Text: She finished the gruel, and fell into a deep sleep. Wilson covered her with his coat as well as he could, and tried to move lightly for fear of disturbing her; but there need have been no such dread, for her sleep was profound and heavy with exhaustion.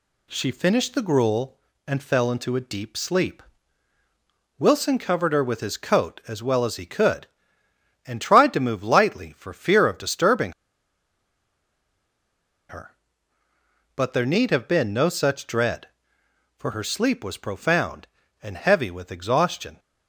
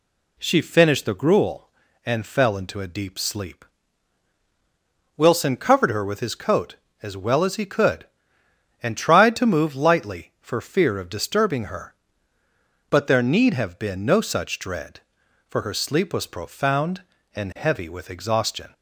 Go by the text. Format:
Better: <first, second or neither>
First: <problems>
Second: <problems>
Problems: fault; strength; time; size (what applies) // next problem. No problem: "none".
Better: second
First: pauses between "disturbing" and "her"; strong; at 10.5 s; 2.1 s long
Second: none